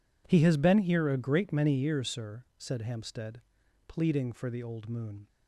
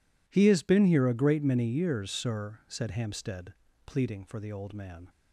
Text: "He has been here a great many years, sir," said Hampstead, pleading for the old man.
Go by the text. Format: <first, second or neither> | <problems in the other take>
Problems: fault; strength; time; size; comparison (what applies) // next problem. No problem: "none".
second | says "moon" for "man"; at 4.8 s